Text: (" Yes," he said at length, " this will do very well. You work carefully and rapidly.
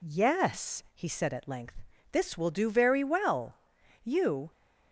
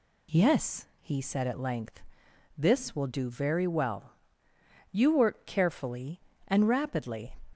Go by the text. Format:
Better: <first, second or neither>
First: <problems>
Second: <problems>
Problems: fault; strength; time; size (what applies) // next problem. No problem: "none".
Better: second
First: stops before "work carefully and rapidly"; at 4.5 s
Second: none